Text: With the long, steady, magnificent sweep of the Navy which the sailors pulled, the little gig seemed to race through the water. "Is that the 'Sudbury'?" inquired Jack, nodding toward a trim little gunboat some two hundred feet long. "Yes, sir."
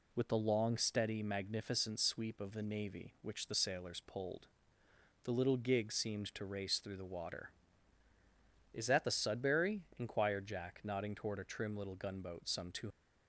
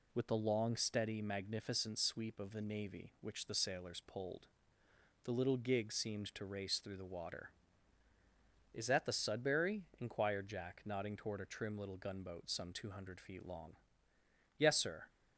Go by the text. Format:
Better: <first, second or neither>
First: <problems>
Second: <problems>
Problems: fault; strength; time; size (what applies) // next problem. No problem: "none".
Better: second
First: stops before "hundred feet long Yes sir"; at 12.8 s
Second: none